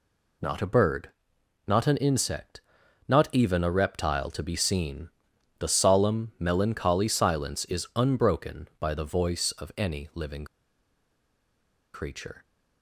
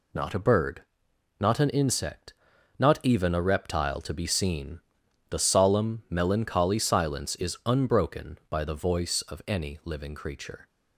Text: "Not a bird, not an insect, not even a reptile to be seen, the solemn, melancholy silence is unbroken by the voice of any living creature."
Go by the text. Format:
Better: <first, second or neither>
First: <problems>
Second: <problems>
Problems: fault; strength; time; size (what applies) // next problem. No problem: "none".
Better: second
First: pauses between "living" and "creature"; strong; at 10.4 s; 1.4 s long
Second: none